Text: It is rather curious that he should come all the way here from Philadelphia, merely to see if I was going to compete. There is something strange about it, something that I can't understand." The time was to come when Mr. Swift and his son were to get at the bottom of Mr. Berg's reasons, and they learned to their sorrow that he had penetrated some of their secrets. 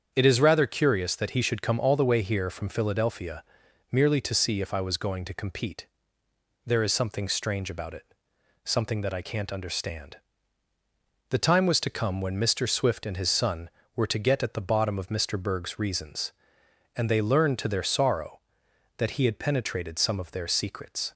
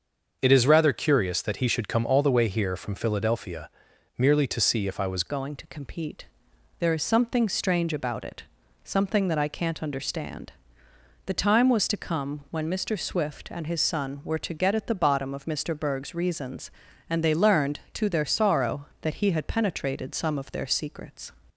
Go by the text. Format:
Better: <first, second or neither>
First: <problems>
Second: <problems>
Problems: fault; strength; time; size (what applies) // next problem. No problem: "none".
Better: first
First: starts louder than the rest; strong; until 1.1 s; 7.5 dB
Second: starts louder than the rest; until 1.4 s; 6.5 dB // changes voice at "going"; from 5.2 s on; 16.1 s long